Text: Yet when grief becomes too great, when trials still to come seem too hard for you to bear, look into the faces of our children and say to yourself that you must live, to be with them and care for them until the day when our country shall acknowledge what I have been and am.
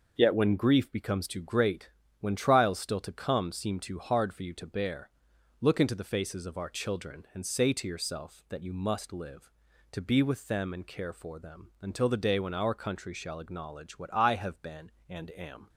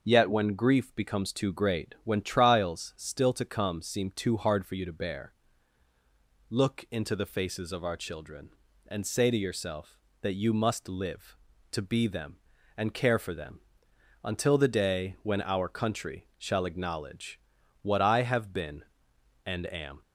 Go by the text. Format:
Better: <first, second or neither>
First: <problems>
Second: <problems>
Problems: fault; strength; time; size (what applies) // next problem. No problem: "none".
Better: first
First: none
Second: starts louder than the rest; noticeable; until 1.0 s; 6 dB // skips "with"; at 12.0 s // pauses between "them" and "until"; noticeable; at 13.5 s; 0.66 s long // pauses between "acknowledge" and "what"; at 17.3 s; 0.42 s long